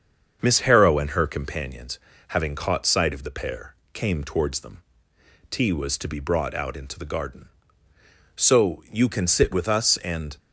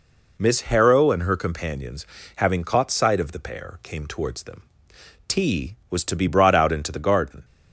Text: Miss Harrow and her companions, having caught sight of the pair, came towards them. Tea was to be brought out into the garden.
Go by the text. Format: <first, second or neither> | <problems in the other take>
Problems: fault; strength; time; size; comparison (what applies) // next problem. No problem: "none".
second | starts louder than the rest; until 1.4 s; 7 dB // goes on to say "So you can sit with us and"; strong; from 8.3 s on; 2.0 s long